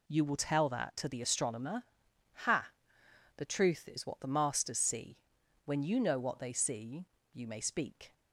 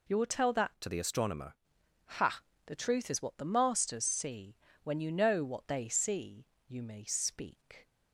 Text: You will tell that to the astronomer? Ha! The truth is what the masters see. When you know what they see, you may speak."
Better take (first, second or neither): first